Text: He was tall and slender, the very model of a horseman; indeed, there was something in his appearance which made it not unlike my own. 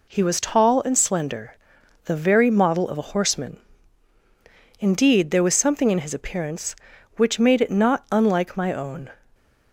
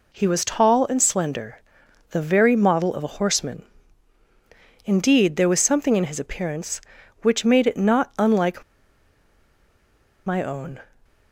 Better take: first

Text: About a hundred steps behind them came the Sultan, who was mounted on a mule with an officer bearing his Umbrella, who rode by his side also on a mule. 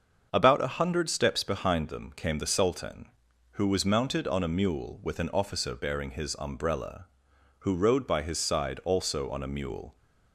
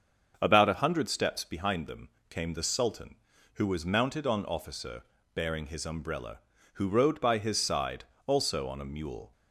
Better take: first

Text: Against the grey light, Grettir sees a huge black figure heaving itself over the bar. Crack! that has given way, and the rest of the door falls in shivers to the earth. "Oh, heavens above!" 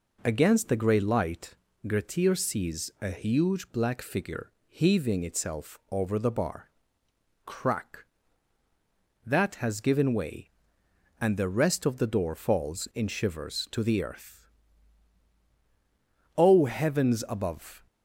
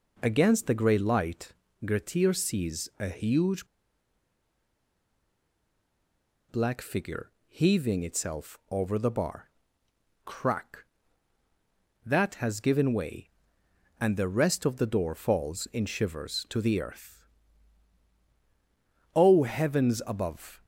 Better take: first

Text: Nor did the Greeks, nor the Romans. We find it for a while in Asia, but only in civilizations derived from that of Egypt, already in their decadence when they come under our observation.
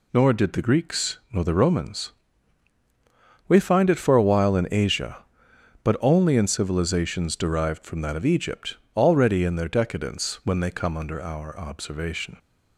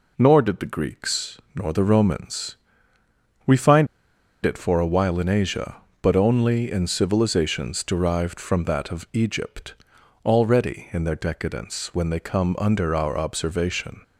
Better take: first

